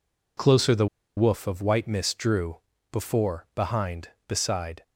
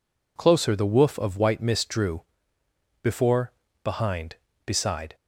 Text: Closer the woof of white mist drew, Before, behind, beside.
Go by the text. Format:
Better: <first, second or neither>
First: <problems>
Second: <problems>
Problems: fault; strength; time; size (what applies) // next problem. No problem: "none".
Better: second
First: pauses between "the" and "woof"; slight; at 0.8 s; 0.30 s long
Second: none